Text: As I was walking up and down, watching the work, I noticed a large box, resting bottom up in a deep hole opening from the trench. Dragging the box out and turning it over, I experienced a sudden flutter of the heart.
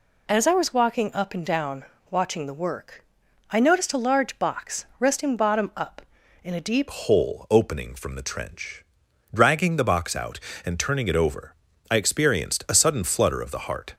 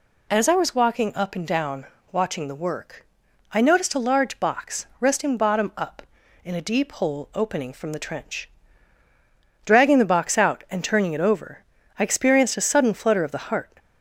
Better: second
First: changes voice at "hole"; from 6.9 s on; 7.0 s long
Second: none

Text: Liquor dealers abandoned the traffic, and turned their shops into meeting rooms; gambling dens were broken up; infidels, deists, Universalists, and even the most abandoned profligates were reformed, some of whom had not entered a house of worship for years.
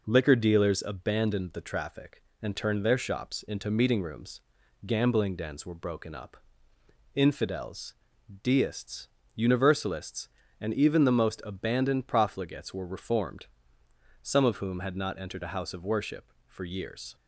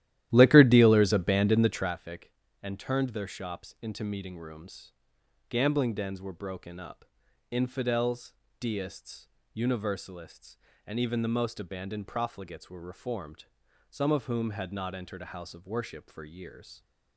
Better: first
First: none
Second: starts louder than the rest; strong; until 1.9 s; 13 dB

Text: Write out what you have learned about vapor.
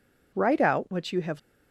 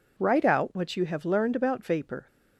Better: second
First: stops before "learned about vapor"; at 1.3 s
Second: none

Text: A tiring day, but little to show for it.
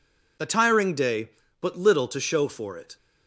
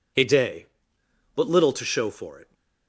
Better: first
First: none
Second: skips "tiring"; at 0.2 s

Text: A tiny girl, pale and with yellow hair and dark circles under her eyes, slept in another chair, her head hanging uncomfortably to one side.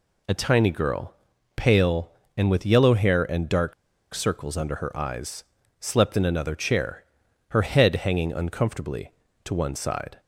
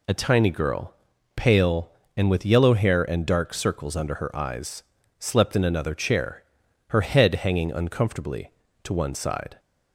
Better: second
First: pauses between "dark" and "circles"; at 3.7 s; 0.40 s long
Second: none

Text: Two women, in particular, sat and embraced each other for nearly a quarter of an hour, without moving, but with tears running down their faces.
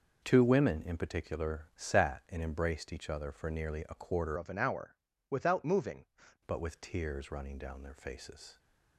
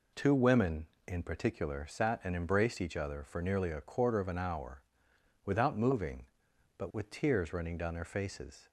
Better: second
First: changes voice from "of" to "moving"; from 4.3 to 6.0 s; 1.7 s long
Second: none

